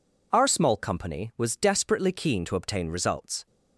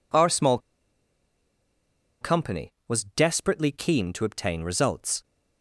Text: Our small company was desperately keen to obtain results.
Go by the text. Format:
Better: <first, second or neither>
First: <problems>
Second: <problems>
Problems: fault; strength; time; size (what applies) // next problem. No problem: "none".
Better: first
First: none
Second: pauses between "small" and "company"; strong; at 0.5 s; 1.6 s long